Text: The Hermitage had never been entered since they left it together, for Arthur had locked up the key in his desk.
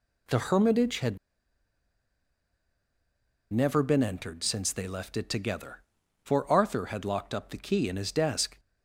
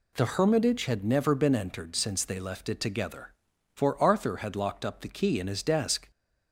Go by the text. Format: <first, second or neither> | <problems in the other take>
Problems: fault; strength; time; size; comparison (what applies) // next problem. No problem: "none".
second | pauses between "had" and "never"; strong; at 1.1 s; 2.3 s long